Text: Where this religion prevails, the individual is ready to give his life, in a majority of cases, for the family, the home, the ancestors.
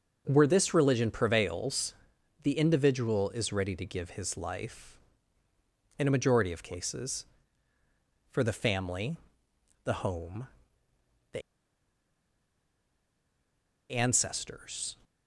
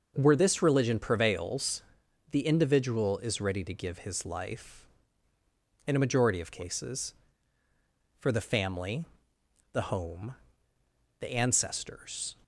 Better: second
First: starts louder than the rest; until 1.2 s; 6.5 dB // pauses between "the" and "ancestors"; strong; at 11.4 s; 2.5 s long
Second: starts louder than the rest; until 1.1 s; 6.5 dB

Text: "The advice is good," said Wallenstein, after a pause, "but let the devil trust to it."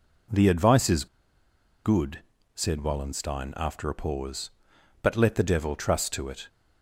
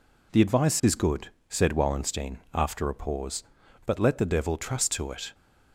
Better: second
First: pauses between "is" and "good"; noticeable; at 1.0 s; 0.79 s long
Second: none

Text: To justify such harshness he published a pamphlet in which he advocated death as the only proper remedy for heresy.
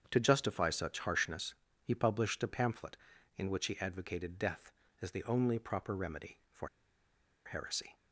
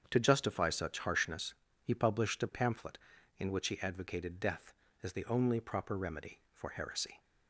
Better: second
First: starts louder than the rest; strong; until 1.1 s; 7.5 dB // pauses between "harshness" and "he"; slight; at 1.5 s; 0.30 s long // pauses between "for" and "heresy"; noticeable; at 6.6 s; 0.77 s long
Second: starts louder than the rest; strong; until 1.1 s; 7.5 dB // pauses between "harshness" and "he"; slight; at 1.5 s; 0.30 s long

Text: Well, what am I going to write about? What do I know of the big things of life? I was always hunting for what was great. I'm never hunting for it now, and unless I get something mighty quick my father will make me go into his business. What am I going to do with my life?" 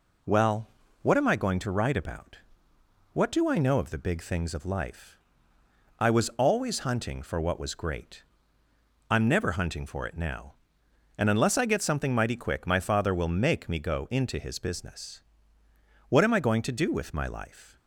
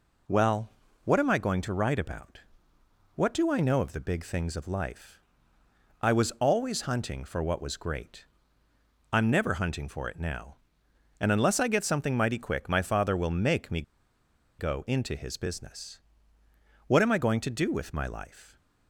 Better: first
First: none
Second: pauses between "me" and "go"; noticeable; at 13.8 s; 0.77 s long

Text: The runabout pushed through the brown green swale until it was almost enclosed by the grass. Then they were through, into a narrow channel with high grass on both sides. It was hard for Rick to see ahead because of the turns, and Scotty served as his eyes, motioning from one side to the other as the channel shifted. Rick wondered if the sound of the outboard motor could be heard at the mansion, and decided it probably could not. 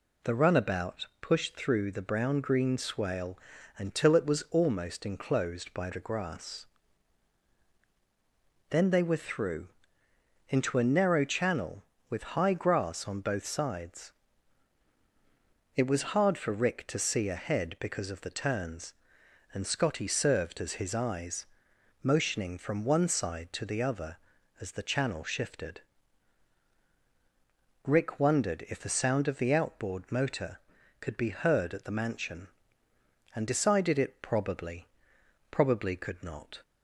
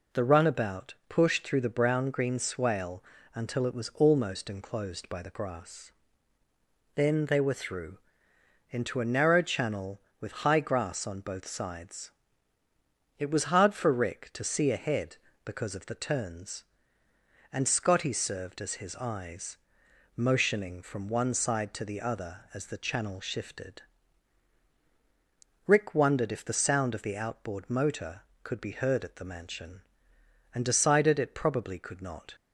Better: second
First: pauses between "swale" and "until"; at 3.3 s; 0.38 s long // says "probably" twice; at 35.5 s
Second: pauses between "swale" and "until"; slight; at 3.0 s; 0.30 s long

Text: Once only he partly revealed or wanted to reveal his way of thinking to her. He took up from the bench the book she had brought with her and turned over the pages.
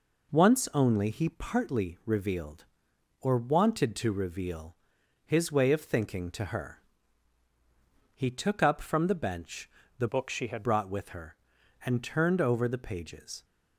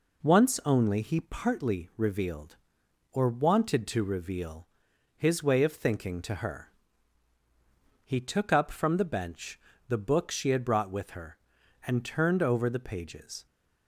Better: second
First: pauses between "reveal" and "his"; noticeable; at 4.7 s; 0.50 s long // pauses between "bench" and "the"; slight; at 9.6 s; 0.30 s long // changes voice from "book" to "had"; from 10.0 to 10.6 s; 0.6 s long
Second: pauses between "reveal" and "his"; noticeable; at 4.6 s; 0.50 s long // pauses between "bench" and "the"; slight; at 9.5 s; 0.30 s long

